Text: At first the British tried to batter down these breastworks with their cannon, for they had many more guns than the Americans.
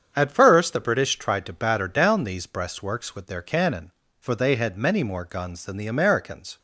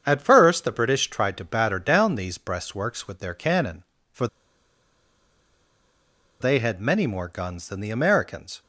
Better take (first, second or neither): first